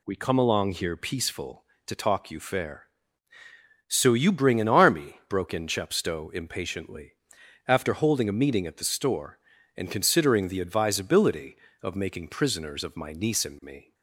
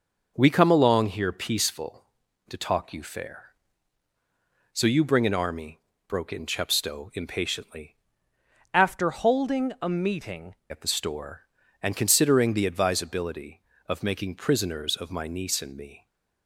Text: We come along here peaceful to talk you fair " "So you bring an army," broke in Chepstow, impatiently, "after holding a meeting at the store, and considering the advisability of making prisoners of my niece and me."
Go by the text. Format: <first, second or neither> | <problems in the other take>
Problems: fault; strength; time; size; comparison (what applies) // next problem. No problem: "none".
first | changes voice from "after" to "meeting"; from 8.7 to 10.5 s; 1.8 s long